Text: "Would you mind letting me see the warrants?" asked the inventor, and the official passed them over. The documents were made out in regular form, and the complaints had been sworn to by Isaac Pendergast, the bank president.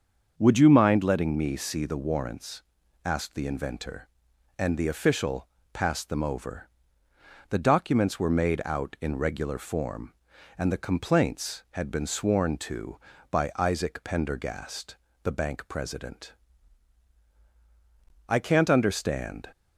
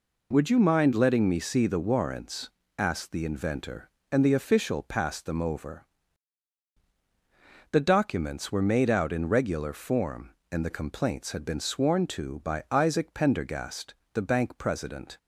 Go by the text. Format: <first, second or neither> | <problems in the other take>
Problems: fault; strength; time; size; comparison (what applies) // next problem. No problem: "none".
second | starts louder than the rest; until 1.3 s; 6.5 dB // pauses between "official" and "passed"; slight; at 5.4 s; 0.24 s long // goes on to say "I can't understand"; noticeable; from 18.2 s on; 1.2 s long